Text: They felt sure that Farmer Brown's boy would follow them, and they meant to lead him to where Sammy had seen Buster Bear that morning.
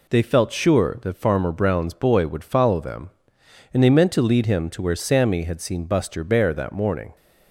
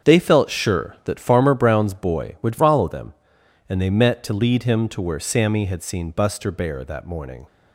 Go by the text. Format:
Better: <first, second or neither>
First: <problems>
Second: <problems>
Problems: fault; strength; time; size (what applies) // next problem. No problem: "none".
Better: first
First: none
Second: starts louder than the rest; strong; until 1.1 s; 7.5 dB // says "met" for "meant"; at 3.8 s